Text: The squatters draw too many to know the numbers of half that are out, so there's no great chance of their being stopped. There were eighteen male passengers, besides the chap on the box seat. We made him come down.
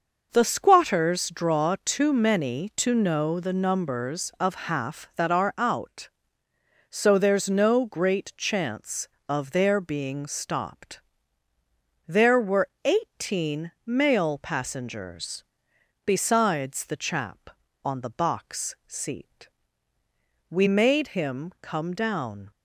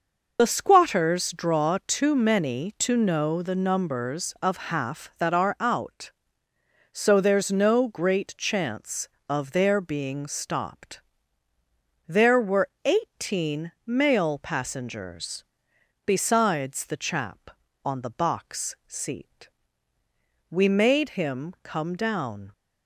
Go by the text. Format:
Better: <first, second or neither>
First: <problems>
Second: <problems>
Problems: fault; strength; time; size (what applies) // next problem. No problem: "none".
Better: first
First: pauses between "were" and "eighteen"; slight; at 12.6 s; 0.16 s long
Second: loses the start of "The"; at 0.3 s; 55 ms // pauses between "were" and "eighteen"; slight; at 12.6 s; 0.16 s long